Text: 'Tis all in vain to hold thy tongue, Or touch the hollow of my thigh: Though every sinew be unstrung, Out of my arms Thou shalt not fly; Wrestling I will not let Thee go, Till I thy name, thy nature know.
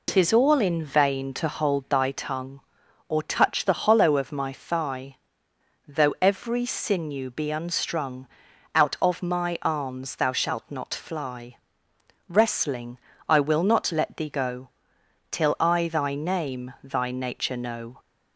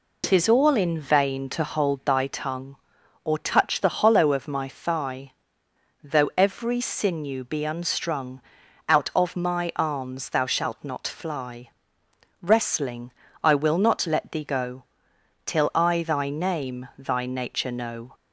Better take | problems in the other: neither | pauses between "Wrestling" and "I"; slight; the same in both

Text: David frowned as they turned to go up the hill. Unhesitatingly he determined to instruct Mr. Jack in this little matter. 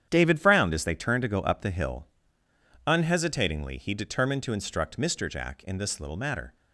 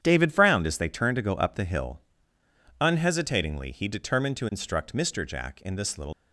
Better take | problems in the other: first | starts louder than the rest; strong; until 1.0 s; 9 dB; strong in the first // stops before "matter"; at 6.1 s

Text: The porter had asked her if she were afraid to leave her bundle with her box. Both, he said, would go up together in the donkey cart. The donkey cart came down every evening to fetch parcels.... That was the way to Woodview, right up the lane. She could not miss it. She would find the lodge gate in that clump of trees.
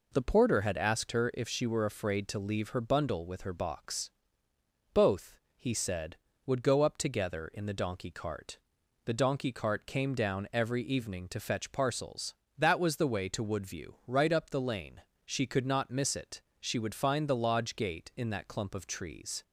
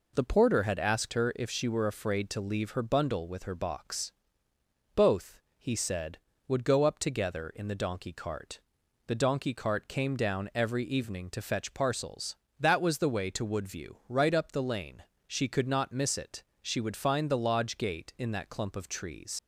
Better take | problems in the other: first | leaves "trees" unfinished; at 19.3 s; 55 ms

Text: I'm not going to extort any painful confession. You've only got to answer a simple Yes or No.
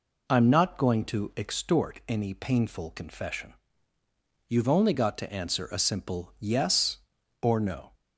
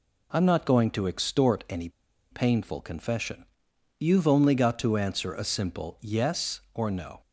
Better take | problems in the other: first | pauses between "any" and "painful"; at 1.8 s; 0.41 s long

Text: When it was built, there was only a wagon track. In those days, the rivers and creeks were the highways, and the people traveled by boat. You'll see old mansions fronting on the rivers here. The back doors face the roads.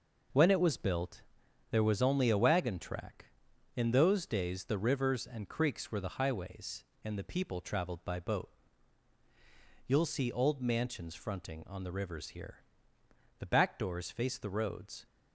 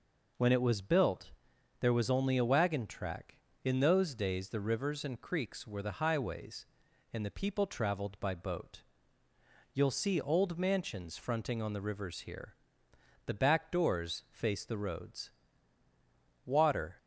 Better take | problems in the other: first | goes on to say "Water"; from 16.4 s on; 0.52 s long

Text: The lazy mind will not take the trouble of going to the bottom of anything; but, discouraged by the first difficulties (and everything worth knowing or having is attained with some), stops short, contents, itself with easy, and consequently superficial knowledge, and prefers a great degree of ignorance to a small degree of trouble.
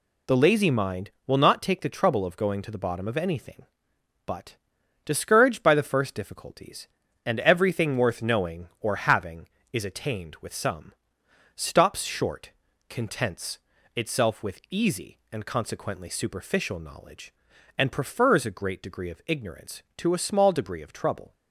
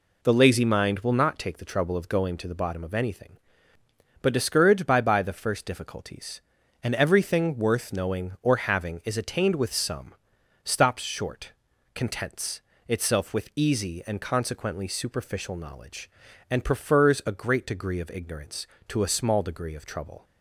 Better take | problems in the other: first | says "by" twice; at 4.9 s

